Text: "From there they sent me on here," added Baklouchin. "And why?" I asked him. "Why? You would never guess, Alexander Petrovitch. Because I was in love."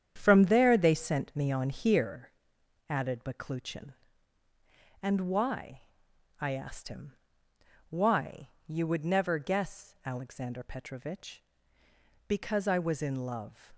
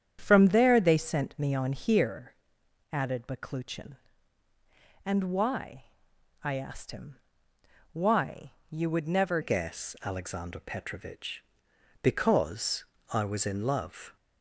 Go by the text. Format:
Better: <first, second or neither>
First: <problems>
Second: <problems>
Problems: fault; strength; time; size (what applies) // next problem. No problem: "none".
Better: first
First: starts louder than the rest; strong; until 1.1 s; 8.5 dB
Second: starts louder than the rest; strong; until 1.2 s; 8.5 dB // changes voice at "guess"; from 9.4 s on; 4.7 s long // pauses between "Because" and "I"; slight; at 12.8 s; 0.28 s long